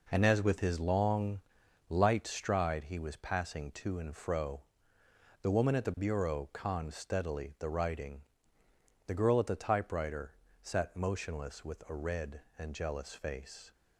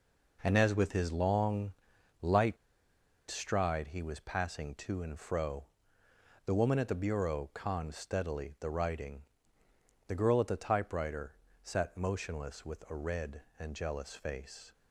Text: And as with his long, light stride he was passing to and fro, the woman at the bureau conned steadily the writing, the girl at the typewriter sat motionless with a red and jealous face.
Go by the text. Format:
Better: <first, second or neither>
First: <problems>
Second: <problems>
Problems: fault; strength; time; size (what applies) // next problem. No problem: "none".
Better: first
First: pauses between "typewriter" and "sat"; slight; at 10.3 s; 0.30 s long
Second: pauses between "light" and "stride"; noticeable; at 2.5 s; 0.74 s long // pauses between "typewriter" and "sat"; slight; at 11.3 s; 0.30 s long